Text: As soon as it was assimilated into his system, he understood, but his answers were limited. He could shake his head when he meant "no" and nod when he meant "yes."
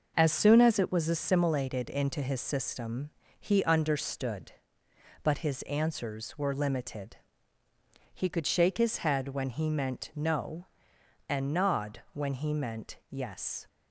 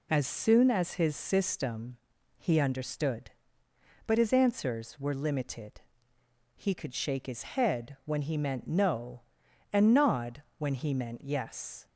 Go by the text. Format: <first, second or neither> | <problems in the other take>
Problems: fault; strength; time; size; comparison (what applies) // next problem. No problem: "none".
first | skips "it was assimilated into"; at 0.9 s // pauses between "nod" and "when"; slight; at 10.4 s; 0.16 s long